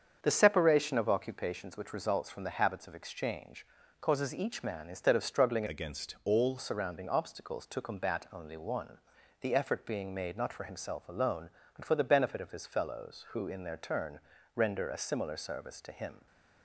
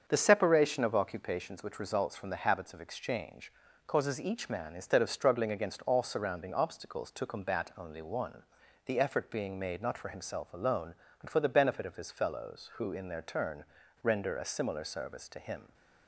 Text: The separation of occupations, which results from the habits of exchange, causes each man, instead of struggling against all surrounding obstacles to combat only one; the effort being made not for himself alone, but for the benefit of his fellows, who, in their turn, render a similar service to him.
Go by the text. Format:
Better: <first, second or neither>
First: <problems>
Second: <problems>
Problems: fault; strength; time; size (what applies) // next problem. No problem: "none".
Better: second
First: starts louder than the rest; strong; until 1.2 s; 7 dB // changes voice from "against" to "all"; from 5.6 to 6.5 s; 0.9 s long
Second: starts louder than the rest; until 1.0 s; 7 dB